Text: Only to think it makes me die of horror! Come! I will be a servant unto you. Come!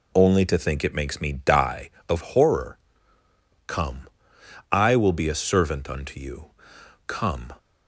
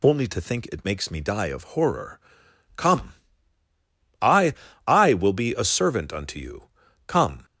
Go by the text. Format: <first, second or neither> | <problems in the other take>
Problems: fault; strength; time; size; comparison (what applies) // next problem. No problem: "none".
first | says "I" twice; at 4.8 s